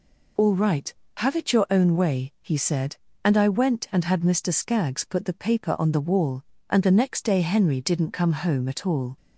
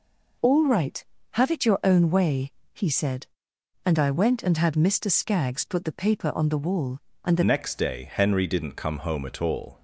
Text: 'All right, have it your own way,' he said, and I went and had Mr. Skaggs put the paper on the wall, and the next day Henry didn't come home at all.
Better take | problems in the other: first | changes voice at "next"; from 7.4 s on; 2.4 s long

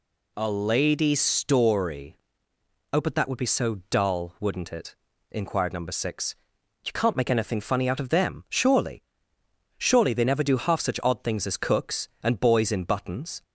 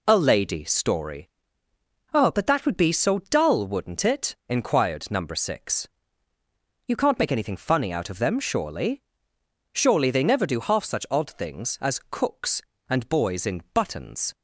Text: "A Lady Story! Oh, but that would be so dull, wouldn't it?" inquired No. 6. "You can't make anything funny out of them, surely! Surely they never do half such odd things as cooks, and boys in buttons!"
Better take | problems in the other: neither | none

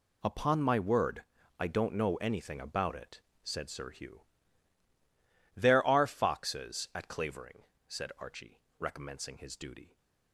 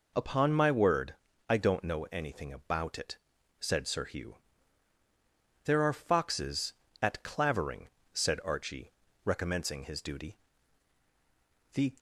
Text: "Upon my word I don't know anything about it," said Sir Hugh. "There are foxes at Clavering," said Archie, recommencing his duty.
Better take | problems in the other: first | pauses between "word" and "I"; slight; at 1.1 s; 0.34 s long; slight in the first // goes on to say "The"; slight; from 11.7 s on; 0.20 s long

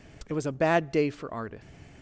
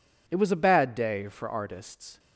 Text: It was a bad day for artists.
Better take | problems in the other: neither | none

